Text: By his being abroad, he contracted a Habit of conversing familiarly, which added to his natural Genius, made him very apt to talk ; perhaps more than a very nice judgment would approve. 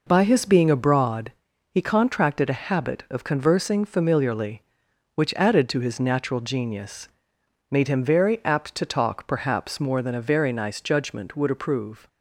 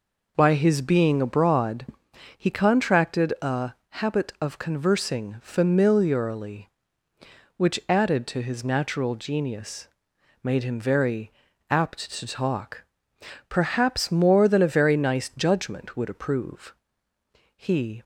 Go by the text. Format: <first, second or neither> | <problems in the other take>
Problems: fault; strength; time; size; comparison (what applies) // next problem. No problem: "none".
first | pauses between "a" and "Habit"; slight; at 3.7 s; 0.20 s long // pauses between "very" and "apt"; at 11.2 s; 0.40 s long // goes on to say "He"; slight; from 17.5 s on; 0.46 s long